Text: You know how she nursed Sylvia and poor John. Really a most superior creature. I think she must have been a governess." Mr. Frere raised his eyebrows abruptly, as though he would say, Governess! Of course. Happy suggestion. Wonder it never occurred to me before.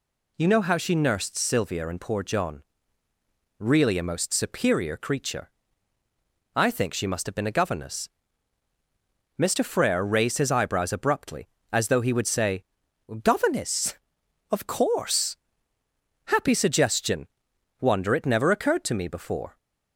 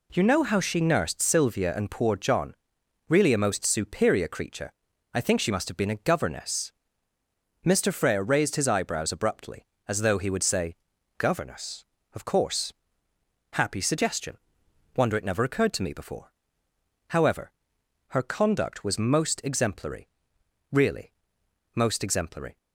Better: first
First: none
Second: goes on to say "However her conduct was most exemplary really most exemplary"; strong; from 17.0 s on; 5.4 s long

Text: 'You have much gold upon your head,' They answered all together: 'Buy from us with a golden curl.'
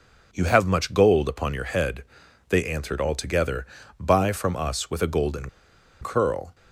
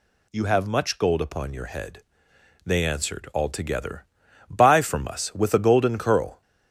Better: second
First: pauses between "golden" and "curl"; noticeable; at 5.4 s; 0.52 s long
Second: none

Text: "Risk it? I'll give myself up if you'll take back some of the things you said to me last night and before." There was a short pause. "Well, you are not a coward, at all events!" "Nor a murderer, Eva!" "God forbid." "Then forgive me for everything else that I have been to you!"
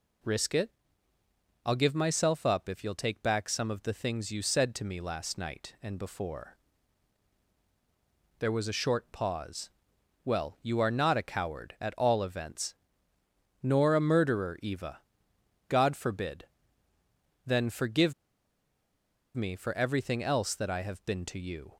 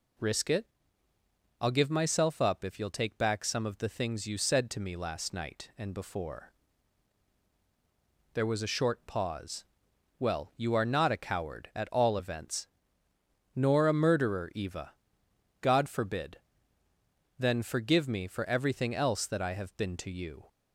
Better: second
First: pauses between "forgive" and "me"; at 18.1 s; 1.2 s long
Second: none

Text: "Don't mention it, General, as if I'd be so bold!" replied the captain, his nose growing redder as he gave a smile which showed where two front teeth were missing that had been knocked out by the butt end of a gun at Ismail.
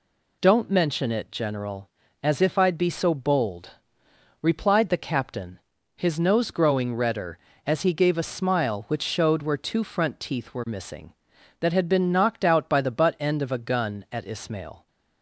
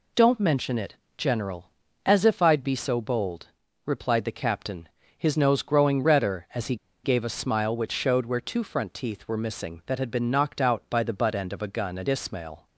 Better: first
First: none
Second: pauses between "he" and "gave"; slight; at 6.7 s; 0.28 s long

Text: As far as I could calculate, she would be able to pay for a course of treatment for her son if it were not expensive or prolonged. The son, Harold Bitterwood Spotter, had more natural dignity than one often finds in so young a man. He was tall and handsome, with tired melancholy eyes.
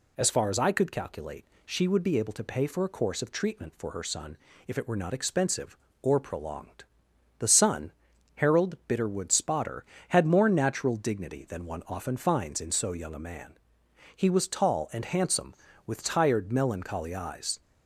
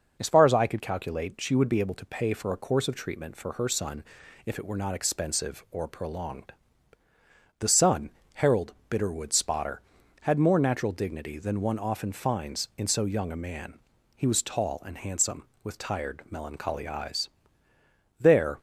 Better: first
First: pauses between "son" and "if"; slight; at 4.3 s; 0.30 s long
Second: pauses between "son" and "if"; at 4.0 s; 0.42 s long // pauses between "Harold" and "Bitterwood"; slight; at 8.7 s; 0.16 s long // goes on to say "There"; slight; from 18.1 s on; 0.40 s long

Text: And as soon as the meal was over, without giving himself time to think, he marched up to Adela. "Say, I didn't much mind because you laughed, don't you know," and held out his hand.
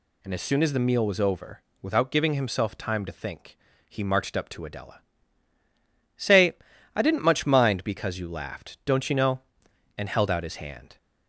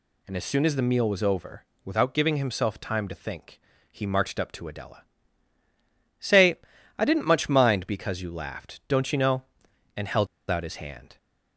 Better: first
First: none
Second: pauses between "held" and "out"; slight; at 10.2 s; 0.24 s long

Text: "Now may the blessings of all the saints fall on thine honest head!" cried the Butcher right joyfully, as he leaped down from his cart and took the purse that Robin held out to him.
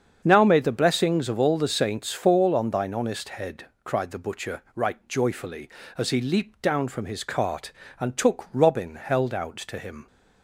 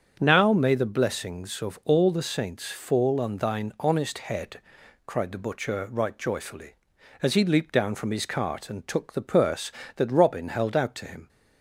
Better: second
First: starts louder than the rest; strong; until 1.2 s; 7 dB // skips "the purse that"; at 8.5 s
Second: starts louder than the rest; strong; until 1.2 s; 7 dB

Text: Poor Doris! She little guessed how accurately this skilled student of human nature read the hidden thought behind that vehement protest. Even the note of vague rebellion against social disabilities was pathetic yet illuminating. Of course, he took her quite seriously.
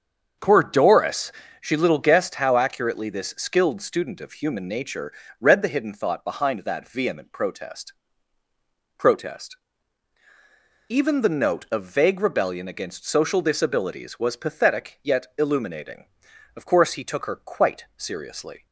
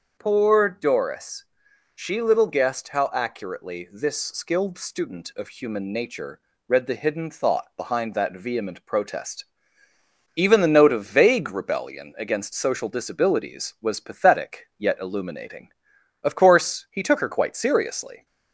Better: second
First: starts louder than the rest; until 1.6 s; 7 dB // pauses between "nature" and "read"; slight; at 5.1 s; 0.30 s long // says "protest" twice; at 8.9 s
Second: starts louder than the rest; until 1.2 s; 6.5 dB // pauses between "nature" and "read"; slight; at 6.3 s; 0.28 s long

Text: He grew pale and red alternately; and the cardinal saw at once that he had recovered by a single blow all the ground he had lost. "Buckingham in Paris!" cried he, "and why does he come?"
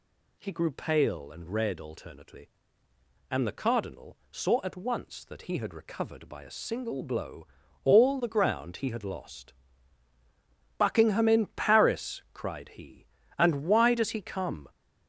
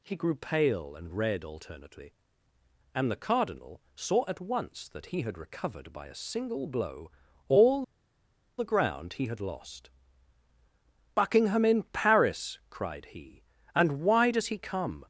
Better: first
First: pauses between "blow" and "all"; at 7.4 s; 0.38 s long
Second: pauses between "blow" and "all"; at 7.0 s; 0.38 s long // pauses between "all" and "the"; noticeable; at 7.8 s; 0.73 s long

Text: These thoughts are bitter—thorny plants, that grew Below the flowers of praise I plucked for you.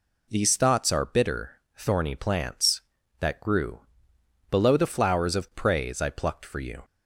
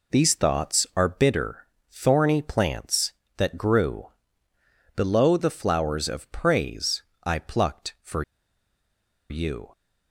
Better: first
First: pauses between "grew" and "Below"; noticeable; at 3.7 s; 0.70 s long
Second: pauses between "grew" and "Below"; noticeable; at 4.0 s; 0.88 s long // pauses between "praise" and "I"; slight; at 7.0 s; 0.20 s long // pauses between "for" and "you"; at 8.2 s; 1.0 s long

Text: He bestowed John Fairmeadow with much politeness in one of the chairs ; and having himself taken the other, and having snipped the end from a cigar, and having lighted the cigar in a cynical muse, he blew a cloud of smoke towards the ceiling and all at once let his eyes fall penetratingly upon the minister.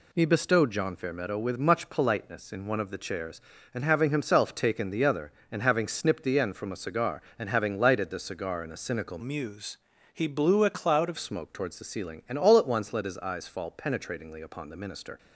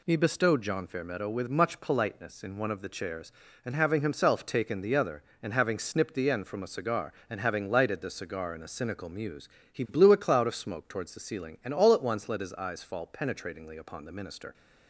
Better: second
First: changes voice from "muse" to "of"; from 9.1 to 11.1 s; 2.0 s long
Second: none

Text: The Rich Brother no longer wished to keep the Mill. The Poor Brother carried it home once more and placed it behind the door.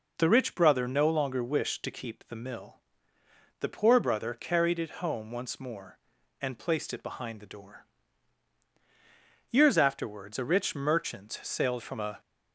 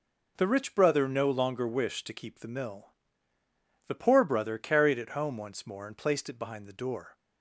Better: second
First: goes on to say "Years afterwards a rich merchant sailed from a"; strong; from 9.4 s on; 2.7 s long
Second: none

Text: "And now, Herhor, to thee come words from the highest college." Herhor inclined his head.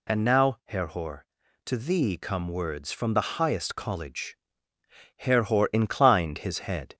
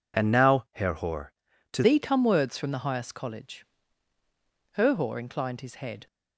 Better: first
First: none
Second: changes voice at "thee"; from 1.8 s on; 4.2 s long

